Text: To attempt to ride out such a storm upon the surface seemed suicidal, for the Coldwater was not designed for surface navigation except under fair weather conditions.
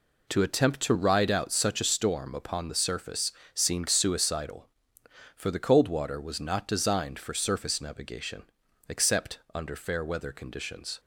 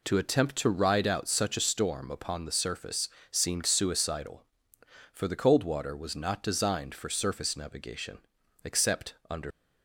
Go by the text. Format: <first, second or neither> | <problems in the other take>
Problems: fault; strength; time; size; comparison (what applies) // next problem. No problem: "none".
first | pauses between "surface" and "seemed"; slight; at 3.0 s; 0.22 s long; slight in the first // pauses between "navigation" and "except"; noticeable; at 8.1 s; 0.46 s long; noticeable in the first // pauses between "except" and "under"; slight; at 9.1 s; 0.16 s long; slight in the first // stops before "fair weather conditions"; at 9.5 s